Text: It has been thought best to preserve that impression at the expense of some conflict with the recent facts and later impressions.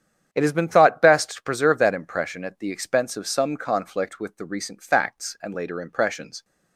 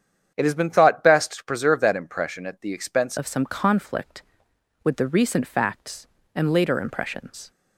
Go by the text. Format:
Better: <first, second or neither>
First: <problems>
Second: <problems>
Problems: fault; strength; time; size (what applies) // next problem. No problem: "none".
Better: first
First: starts louder than the rest; strong; until 1.3 s; 9 dB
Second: starts louder than the rest; strong; until 1.3 s; 8.5 dB // changes voice at "of"; from 3.1 s on; 4.4 s long